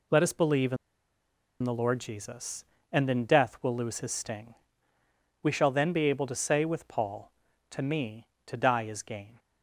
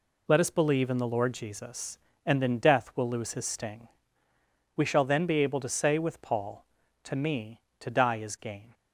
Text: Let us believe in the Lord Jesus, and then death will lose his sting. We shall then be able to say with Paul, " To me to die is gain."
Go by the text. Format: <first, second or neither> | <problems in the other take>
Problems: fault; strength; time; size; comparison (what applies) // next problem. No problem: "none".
second | pauses between "in" and "the"; noticeable; at 0.7 s; 0.86 s long